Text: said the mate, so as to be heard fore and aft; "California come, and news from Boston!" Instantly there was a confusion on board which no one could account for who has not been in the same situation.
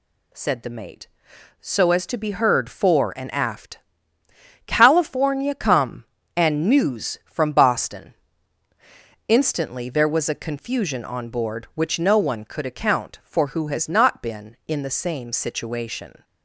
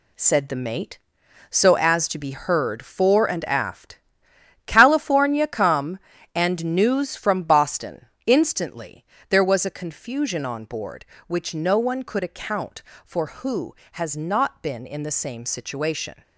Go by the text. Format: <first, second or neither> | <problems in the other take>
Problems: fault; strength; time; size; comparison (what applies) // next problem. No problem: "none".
first | gets quieter; strong; throughout; 7.5 dB // pauses between "Instantly" and "there"; slight; at 9.0 s; 0.26 s long